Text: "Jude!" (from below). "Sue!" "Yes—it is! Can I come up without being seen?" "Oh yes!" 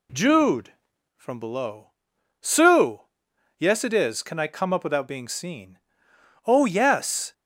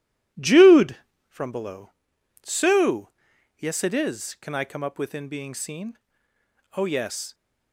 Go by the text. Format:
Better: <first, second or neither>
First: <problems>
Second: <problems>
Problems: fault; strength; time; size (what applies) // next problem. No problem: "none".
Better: first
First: none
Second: says "within" for "without"; at 4.9 s